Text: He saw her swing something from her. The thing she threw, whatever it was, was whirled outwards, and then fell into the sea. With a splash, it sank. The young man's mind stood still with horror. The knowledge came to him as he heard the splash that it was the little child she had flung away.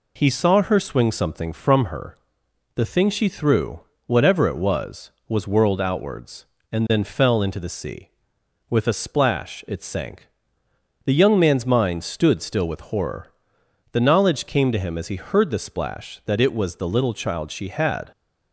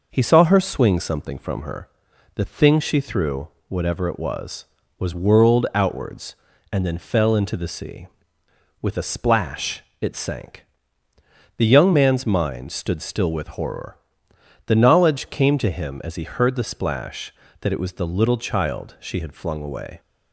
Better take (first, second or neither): second